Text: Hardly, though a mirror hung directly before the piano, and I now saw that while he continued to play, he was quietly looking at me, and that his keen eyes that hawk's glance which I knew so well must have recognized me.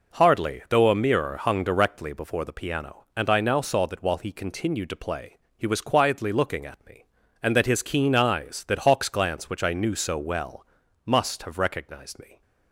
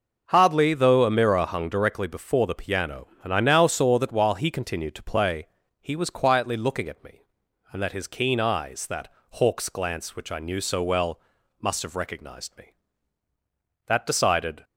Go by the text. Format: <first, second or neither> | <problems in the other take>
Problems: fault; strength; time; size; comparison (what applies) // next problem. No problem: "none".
first | pauses between "that" and "hawk's"; slight; at 9.0 s; 0.22 s long // pauses between "well" and "must"; at 11.1 s; 0.40 s long; also in the first // goes on to say "That decided"; noticeable; from 13.8 s on; 0.76 s long